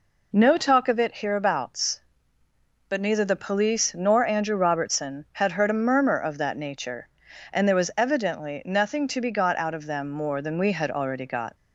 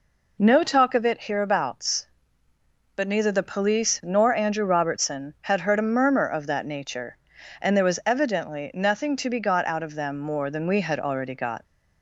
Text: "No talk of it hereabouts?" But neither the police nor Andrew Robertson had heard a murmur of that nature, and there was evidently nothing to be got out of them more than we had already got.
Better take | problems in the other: neither | none

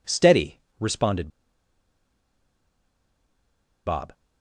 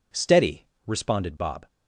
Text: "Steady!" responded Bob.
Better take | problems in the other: second | pauses between "responded" and "Bob"; strong; at 1.2 s; 2.5 s long

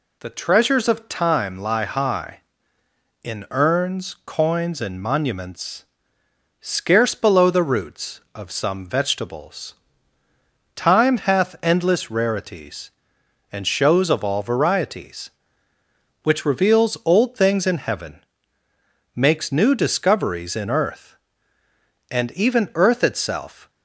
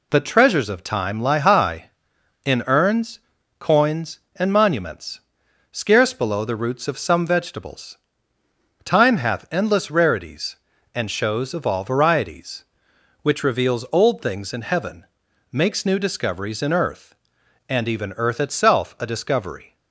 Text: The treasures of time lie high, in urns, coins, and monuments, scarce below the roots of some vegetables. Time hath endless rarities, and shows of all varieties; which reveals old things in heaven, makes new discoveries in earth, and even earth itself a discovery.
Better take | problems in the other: second | stops before "a discovery"; at 23.6 s

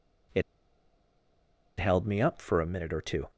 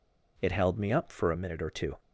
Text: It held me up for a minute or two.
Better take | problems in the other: second | pauses between "It" and "held"; strong; at 0.4 s; 1.3 s long

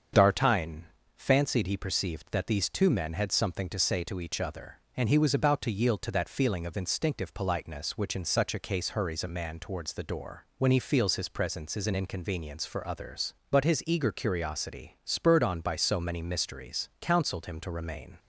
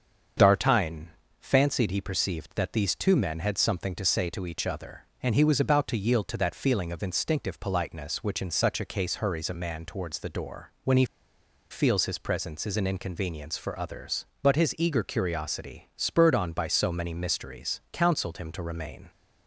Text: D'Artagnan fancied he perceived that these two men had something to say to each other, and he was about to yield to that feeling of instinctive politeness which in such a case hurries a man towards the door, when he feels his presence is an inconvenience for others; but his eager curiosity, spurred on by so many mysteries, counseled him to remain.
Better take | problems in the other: first | starts louder than the rest; until 1.6 s; 7 dB; strong in the first // pauses between "D'Artagnan" and "fancied"; slight; at 1.1 s; 0.30 s long; slight in the first // pauses between "he" and "feels"; noticeable; at 11.0 s; 0.66 s long

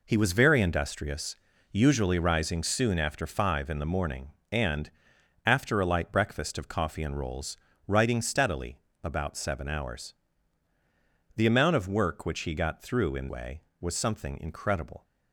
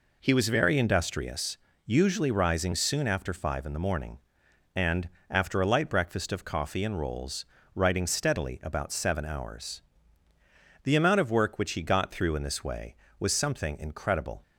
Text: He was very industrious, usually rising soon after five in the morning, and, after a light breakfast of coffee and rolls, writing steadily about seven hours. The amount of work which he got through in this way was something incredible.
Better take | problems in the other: second | pauses between "steadily" and "about"; slight; at 8.7 s; 0.24 s long // skips "this"; at 13.2 s

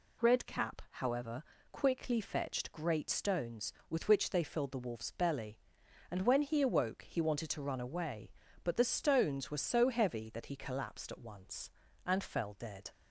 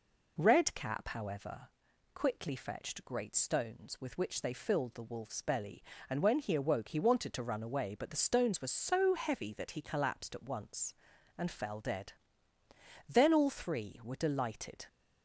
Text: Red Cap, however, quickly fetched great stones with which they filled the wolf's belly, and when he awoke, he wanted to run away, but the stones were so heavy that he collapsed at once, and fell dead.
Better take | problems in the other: first | goes on to say "Then all three were delighted"; strong; from 13.0 s on; 1.7 s long

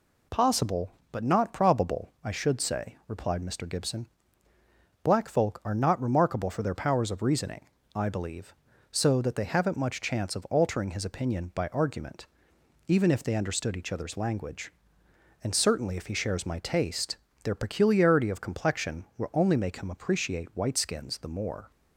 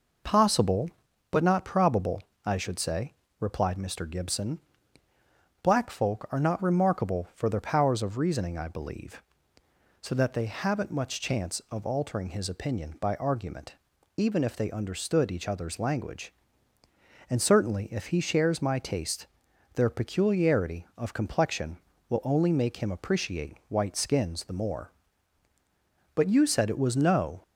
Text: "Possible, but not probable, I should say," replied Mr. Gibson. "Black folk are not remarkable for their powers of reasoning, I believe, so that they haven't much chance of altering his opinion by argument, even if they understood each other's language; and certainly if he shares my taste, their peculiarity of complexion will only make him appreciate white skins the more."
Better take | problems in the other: first | goes on to say "But you said it was no"; noticeable; from 26.1 s on; 1.2 s long

